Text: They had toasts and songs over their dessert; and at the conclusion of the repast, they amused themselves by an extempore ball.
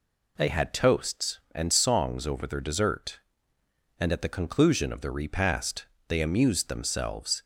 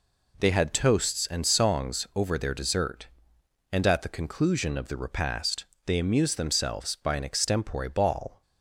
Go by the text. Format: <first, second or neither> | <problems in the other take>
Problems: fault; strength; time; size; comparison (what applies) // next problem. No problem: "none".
second | stops before "by an extempore ball"; at 7.4 s